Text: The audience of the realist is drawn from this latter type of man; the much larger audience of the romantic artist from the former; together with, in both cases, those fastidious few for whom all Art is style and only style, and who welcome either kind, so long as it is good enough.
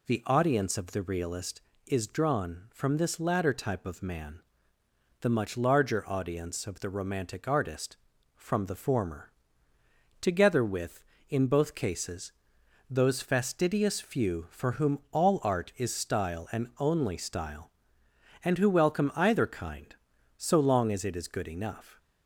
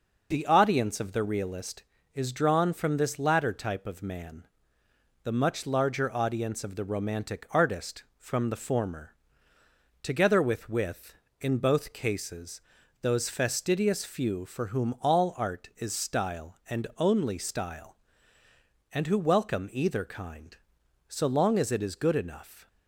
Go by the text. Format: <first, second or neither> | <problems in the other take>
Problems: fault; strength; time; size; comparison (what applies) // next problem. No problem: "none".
first | says "with" twice; at 10.6 s